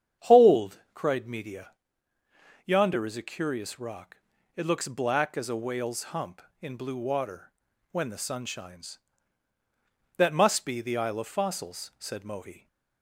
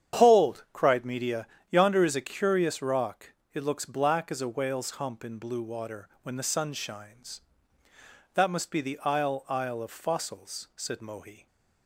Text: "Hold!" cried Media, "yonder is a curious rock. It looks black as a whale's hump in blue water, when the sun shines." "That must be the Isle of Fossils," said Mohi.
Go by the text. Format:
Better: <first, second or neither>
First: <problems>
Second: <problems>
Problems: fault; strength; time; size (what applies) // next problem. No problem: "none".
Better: first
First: starts louder than the rest; strong; until 1.3 s; 8.5 dB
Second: starts louder than the rest; strong; until 1.2 s; 9 dB // says "Isle" twice; at 9.4 s